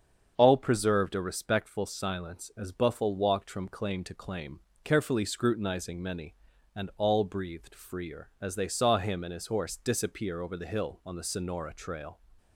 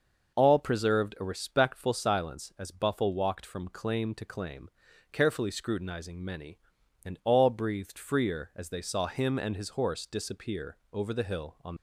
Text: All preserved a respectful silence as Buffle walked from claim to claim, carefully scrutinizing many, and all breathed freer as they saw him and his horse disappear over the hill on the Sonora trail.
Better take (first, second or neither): first